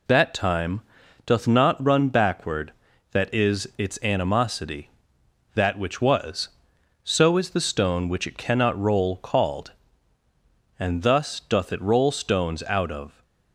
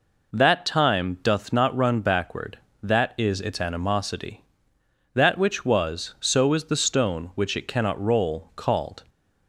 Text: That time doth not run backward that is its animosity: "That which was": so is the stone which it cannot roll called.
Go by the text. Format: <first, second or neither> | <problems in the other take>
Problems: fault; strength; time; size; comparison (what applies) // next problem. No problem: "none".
second | pauses between "time" and "doth"; at 0.8 s; 0.44 s long // goes on to say "And thus doth it roll stones out of"; strong; from 10.7 s on; 2.4 s long